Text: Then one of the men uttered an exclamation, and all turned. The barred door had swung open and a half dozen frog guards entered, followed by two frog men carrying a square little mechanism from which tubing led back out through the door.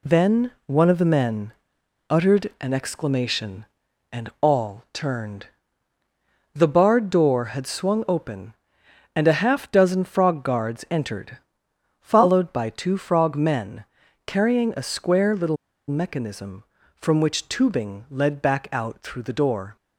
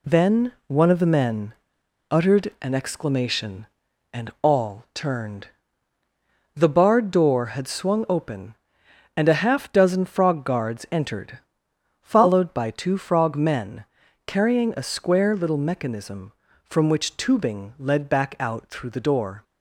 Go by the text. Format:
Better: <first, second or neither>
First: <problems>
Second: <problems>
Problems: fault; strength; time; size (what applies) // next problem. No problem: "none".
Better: second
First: pauses between "Then" and "one"; slight; at 0.5 s; 0.16 s long // pauses between "men" and "uttered"; noticeable; at 1.5 s; 0.58 s long // pauses between "men" and "carrying"; at 13.8 s; 0.42 s long // pauses between "little" and "mechanism"; slight; at 15.5 s; 0.31 s long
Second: pauses between "Then" and "one"; slight; at 0.5 s; 0.16 s long // pauses between "men" and "uttered"; noticeable; at 1.5 s; 0.58 s long // pauses between "men" and "carrying"; at 13.8 s; 0.42 s long